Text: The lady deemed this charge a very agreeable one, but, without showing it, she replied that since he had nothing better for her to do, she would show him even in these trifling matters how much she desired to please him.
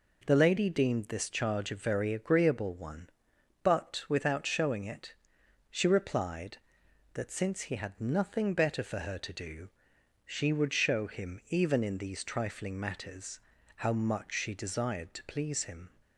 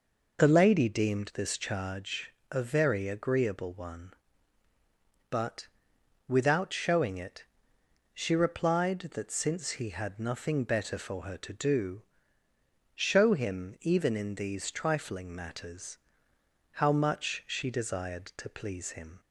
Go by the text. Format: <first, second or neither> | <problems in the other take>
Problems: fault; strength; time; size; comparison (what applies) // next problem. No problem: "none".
first | pauses between "charge" and "a"; slight; at 2.3 s; 0.18 s long // skips "she would"; at 12.4 s // pauses between "matters" and "how"; noticeable; at 15.9 s; 0.74 s long; slight in the first